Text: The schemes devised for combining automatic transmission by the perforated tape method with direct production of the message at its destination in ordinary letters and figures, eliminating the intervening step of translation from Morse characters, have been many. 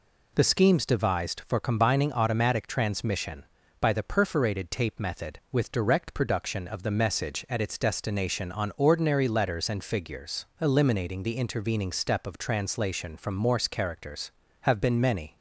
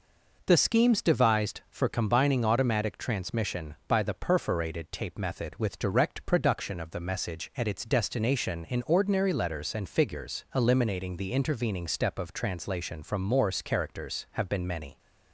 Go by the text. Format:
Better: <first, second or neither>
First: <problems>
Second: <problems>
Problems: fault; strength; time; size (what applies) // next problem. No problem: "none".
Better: second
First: says "on" for "in"; at 8.5 s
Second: none